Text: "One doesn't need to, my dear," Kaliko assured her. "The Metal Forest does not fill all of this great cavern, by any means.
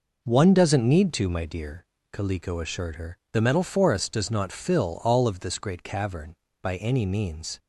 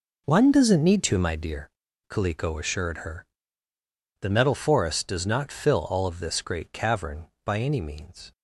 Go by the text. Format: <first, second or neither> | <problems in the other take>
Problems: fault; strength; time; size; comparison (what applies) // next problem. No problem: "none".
first | gets quieter; strong; throughout; 11.5 dB